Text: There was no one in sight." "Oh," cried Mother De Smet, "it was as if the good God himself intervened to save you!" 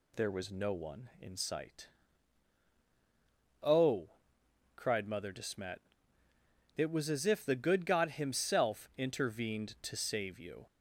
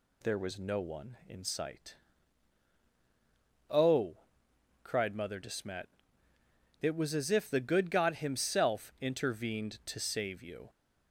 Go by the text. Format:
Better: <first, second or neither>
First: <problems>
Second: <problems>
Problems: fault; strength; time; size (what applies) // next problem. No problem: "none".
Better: neither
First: none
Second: none